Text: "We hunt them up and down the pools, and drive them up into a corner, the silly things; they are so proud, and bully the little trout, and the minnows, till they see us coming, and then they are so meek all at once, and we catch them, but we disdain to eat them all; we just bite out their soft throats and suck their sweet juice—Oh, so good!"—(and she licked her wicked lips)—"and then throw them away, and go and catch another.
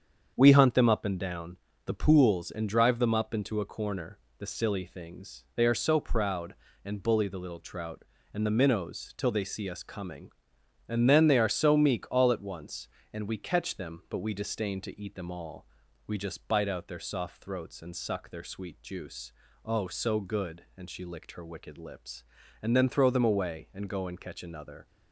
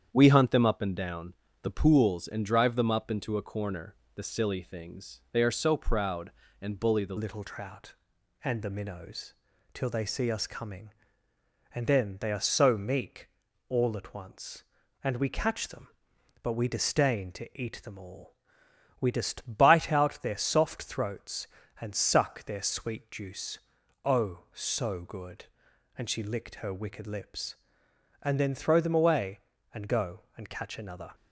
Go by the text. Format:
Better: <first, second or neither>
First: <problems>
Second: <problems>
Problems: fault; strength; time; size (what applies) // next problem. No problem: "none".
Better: first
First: starts louder than the rest; strong; until 1.3 s; 7.5 dB // pauses between "down" and "the"; slight; at 1.5 s; 0.28 s long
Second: starts louder than the rest; strong; until 1.1 s; 8.5 dB // pauses between "down" and "the"; slight; at 1.3 s; 0.28 s long // changes voice at "little"; from 7.1 s on; 24.0 s long // pauses between "meek" and "all"; at 13.2 s; 0.40 s long